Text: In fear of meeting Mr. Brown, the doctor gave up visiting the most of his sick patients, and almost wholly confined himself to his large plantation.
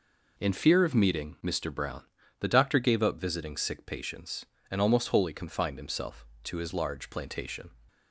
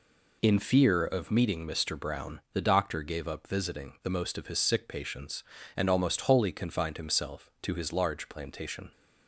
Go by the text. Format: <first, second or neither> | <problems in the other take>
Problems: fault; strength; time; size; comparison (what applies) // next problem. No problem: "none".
second | skips "the most of his"; at 3.5 s